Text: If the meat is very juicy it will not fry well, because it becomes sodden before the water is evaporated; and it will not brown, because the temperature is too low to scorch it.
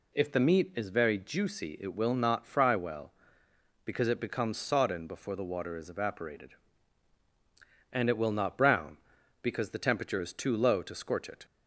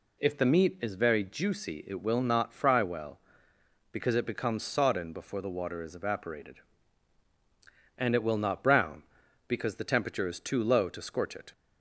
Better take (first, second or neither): neither